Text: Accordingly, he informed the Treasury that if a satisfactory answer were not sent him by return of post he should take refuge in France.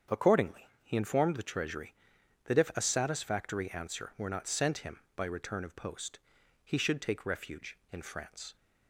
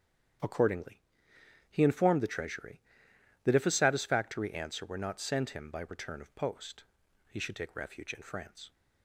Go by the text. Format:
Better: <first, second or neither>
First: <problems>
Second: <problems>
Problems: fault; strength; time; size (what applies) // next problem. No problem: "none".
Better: neither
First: starts louder than the rest; strong; until 1.2 s; 7.5 dB // pauses between "post" and "he"; noticeable; at 6.1 s; 0.46 s long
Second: starts louder than the rest; strong; until 2.0 s; 9 dB // pauses between "post" and "he"; noticeable; at 6.8 s; 0.46 s long